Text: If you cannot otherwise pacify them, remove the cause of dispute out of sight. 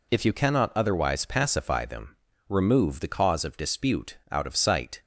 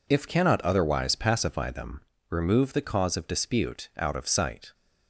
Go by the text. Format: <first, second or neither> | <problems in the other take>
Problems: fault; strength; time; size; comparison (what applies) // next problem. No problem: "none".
first | skips "you"; at 0.2 s